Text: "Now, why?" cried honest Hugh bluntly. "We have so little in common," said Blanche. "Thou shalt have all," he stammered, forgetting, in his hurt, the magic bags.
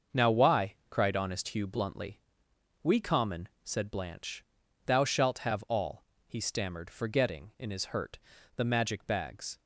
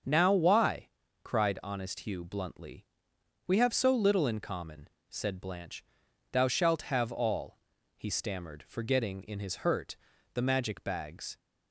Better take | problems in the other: second | starts louder than the rest; until 1.2 s; 6.5 dB; also in the second // skips "have so little in"; at 2.9 s

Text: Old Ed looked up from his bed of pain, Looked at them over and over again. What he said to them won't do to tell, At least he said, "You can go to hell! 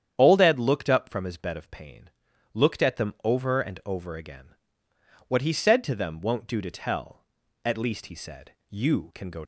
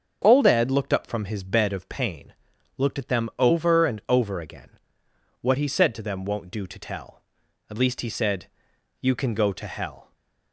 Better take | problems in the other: second | starts louder than the rest; strong; until 1.1 s; 9 dB; also in the second // stops before "to hell"; at 9.4 s

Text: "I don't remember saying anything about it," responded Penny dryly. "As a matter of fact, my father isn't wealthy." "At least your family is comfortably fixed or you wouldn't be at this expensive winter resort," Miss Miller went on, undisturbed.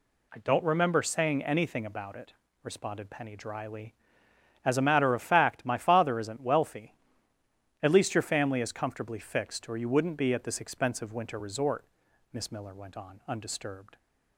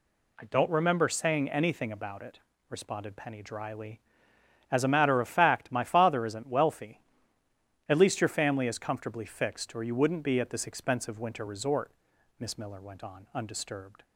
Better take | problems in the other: neither | none

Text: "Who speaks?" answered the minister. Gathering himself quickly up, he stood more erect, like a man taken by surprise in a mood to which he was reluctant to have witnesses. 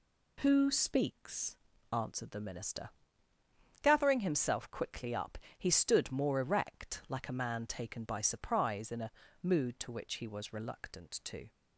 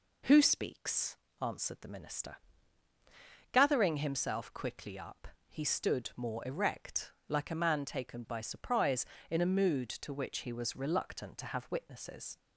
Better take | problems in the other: second | pauses between "a" and "mood"; slight; at 9.1 s; 0.32 s long // stops before "have witnesses"; at 11.5 s

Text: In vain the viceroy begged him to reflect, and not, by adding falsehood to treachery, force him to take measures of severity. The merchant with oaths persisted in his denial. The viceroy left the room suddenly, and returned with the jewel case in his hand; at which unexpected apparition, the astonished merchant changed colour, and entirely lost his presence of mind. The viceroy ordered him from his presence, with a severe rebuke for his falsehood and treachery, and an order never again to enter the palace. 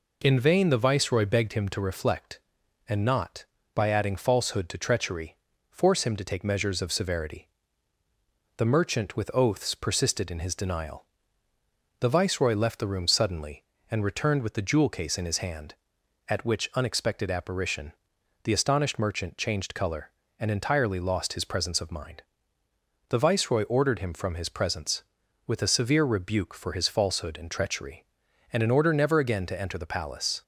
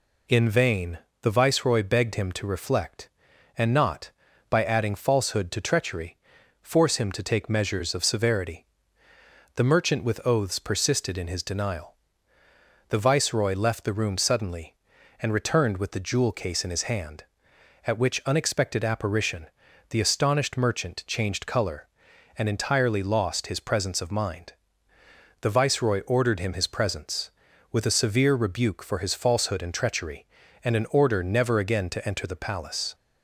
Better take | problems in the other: first | pauses between "vain" and "the"; slight; at 0.9 s; 0.24 s long // skips "from"; at 26.5 s

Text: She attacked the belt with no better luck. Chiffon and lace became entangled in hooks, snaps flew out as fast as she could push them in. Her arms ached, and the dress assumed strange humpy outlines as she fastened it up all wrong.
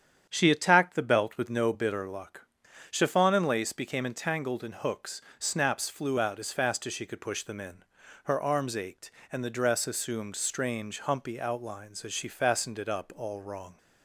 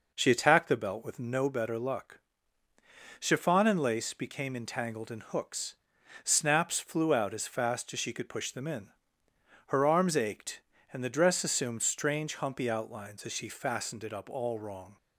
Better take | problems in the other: second | starts louder than the rest; strong; until 1.2 s; 9 dB // says "bitter" for "better"; at 1.7 s

